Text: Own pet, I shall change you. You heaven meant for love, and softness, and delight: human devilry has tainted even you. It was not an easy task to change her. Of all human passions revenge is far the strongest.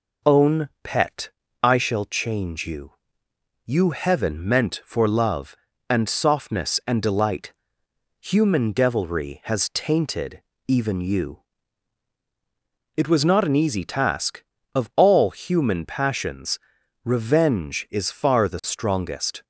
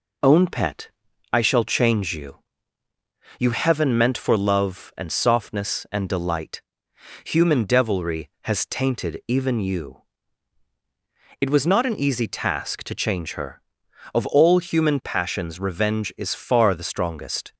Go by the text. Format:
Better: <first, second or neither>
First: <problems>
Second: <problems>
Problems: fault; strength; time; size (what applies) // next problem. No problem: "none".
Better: second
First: pauses between "Own" and "pet"; slight; at 0.6 s; 0.16 s long // pauses between "tainted" and "even"; slight; at 10.4 s; 0.28 s long // skips "to change her"; at 14.5 s // pauses between "passions" and "revenge"; noticeable; at 16.5 s; 0.46 s long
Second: none